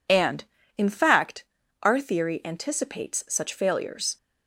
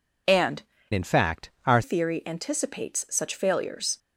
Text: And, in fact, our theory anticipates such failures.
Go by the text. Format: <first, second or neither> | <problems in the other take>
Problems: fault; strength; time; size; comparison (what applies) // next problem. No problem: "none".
first | changes voice from "in" to "our"; from 0.9 to 1.8 s; 0.9 s long